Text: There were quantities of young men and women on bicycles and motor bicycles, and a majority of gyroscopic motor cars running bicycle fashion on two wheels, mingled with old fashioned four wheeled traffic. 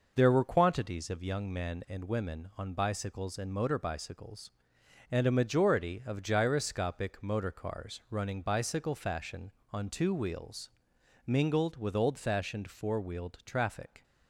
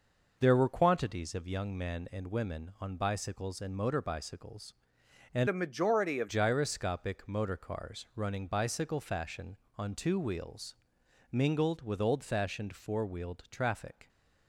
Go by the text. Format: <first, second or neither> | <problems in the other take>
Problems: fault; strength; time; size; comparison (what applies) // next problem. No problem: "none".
first | changes voice from "a" to "of"; from 5.4 to 6.2 s; 0.8 s long